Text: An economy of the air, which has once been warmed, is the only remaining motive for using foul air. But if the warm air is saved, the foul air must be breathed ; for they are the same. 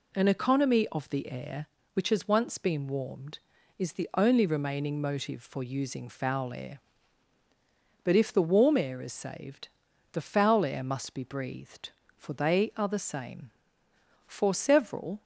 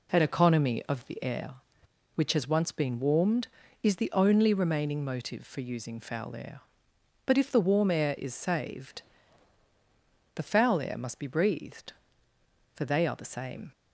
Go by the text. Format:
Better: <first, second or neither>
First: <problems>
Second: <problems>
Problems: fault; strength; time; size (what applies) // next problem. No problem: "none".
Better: second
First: goes on to say "For several"; noticeable; from 14.2 s on; 0.96 s long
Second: none